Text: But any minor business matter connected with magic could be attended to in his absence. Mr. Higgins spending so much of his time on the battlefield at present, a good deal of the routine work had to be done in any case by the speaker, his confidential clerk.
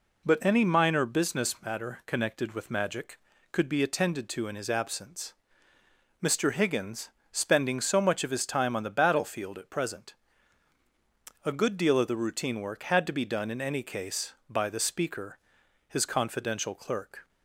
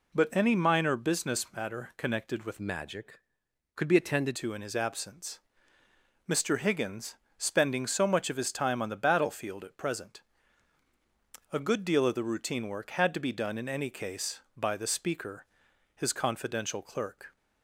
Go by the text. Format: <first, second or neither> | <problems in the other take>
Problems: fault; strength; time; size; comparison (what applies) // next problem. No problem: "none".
first | changes voice from "magic" to "attended"; from 2.5 to 4.3 s; 1.8 s long // pauses between "Higgins" and "spending"; slight; at 7.1 s; 0.22 s long; slight in the first